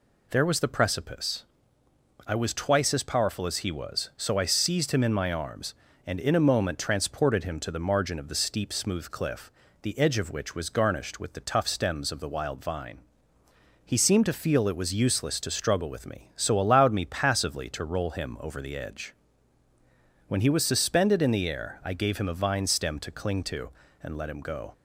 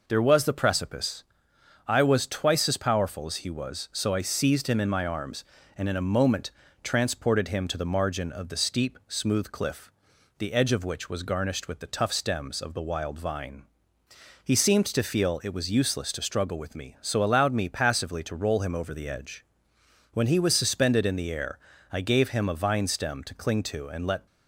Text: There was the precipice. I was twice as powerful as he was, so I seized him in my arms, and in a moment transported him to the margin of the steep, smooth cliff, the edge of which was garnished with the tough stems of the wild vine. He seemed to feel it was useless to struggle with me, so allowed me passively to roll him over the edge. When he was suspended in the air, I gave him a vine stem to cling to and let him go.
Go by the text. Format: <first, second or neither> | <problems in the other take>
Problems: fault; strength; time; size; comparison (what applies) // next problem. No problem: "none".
first | pauses between "moment" and "transported"; slight; at 6.5 s; 0.32 s long // stops before "him go"; at 24.2 s